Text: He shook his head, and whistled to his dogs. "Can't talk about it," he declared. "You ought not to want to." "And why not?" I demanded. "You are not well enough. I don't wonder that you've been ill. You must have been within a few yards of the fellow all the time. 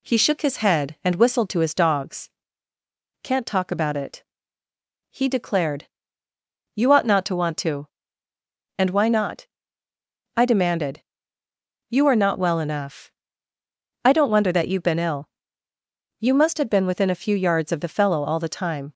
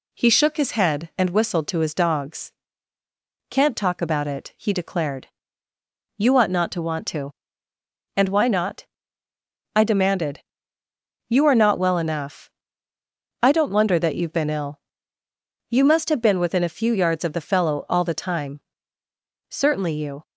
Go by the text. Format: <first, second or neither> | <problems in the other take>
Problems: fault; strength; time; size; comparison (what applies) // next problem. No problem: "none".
first | goes on to say "Certainly you"; noticeable; from 19.4 s on; 0.74 s long